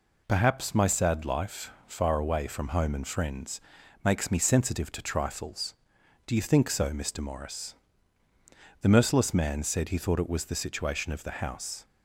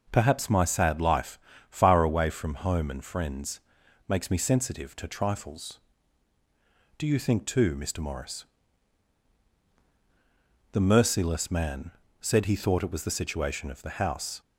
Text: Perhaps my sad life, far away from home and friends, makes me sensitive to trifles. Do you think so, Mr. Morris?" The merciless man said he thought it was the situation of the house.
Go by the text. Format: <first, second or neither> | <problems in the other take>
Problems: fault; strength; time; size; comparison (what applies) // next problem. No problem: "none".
first | says "too" for "so"; at 7.4 s // pauses between "man" and "said"; slight; at 11.9 s; 0.32 s long